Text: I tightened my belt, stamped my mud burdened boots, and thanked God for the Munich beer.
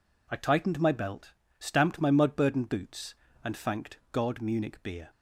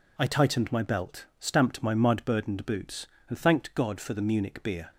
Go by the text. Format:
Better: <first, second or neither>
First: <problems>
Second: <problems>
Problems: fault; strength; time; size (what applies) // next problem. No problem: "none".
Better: second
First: skips "for the"; at 4.4 s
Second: none